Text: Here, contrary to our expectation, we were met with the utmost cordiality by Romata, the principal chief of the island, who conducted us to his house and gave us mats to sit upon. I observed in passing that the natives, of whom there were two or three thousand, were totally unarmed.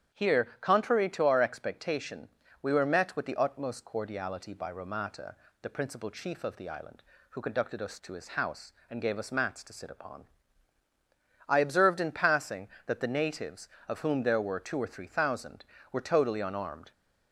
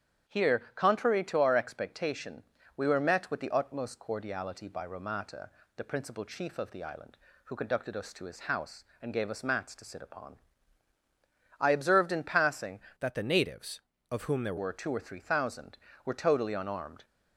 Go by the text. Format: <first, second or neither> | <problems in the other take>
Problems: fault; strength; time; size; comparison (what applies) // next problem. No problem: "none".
first | starts louder than the rest; strong; until 1.3 s; 9.5 dB; strong in the first // changes voice from "that" to "there"; from 12.9 to 14.5 s; 1.6 s long